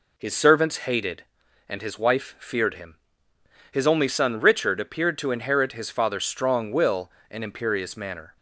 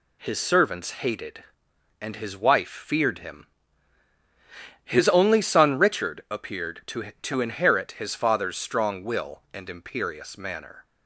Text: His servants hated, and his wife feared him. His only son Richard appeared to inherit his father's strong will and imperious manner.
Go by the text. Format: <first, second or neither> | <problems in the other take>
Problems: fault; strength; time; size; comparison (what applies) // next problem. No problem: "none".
first | says "to" twice; at 7.2 s